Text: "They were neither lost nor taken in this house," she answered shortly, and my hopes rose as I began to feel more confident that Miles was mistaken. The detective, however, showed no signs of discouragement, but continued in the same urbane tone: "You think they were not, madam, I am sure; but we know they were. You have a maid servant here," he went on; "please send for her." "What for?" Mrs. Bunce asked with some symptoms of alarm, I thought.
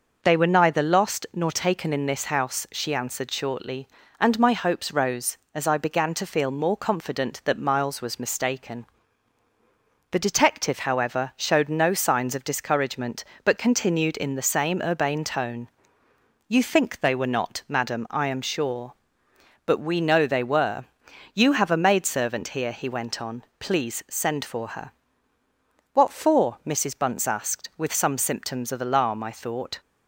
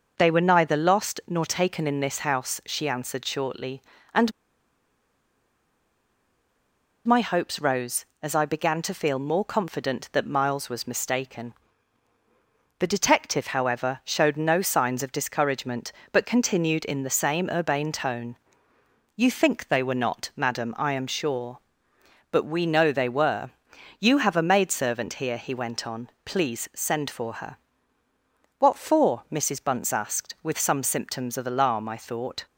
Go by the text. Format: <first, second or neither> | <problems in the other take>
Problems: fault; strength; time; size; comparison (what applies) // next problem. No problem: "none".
first | pauses between "and" and "my"; strong; at 4.3 s; 2.7 s long